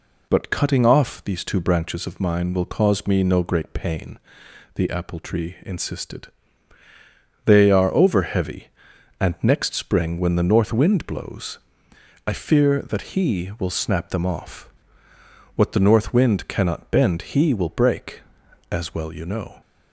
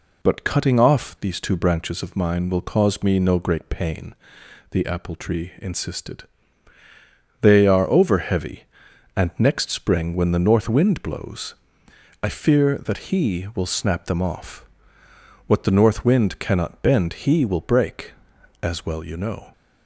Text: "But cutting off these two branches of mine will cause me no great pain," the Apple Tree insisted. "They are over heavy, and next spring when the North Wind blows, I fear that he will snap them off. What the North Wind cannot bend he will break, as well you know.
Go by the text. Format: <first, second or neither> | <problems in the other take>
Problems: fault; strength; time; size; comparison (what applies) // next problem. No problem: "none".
neither | none